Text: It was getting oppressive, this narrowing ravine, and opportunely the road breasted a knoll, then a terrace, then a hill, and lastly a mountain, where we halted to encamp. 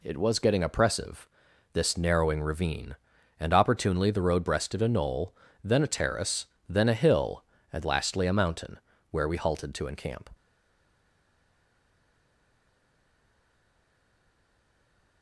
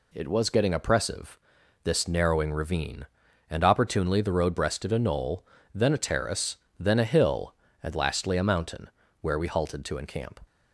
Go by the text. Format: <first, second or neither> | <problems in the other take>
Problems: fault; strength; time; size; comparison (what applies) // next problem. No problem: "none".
second | stays silent after the last word; strong; from 10.3 s on; 4.9 s long